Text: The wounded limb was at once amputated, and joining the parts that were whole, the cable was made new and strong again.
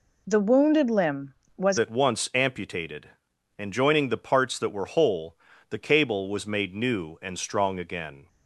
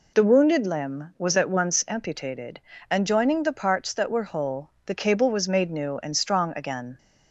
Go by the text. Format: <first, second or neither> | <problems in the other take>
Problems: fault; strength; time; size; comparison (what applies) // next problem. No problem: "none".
second | changes voice at "at"; from 1.7 s on; 6.5 s long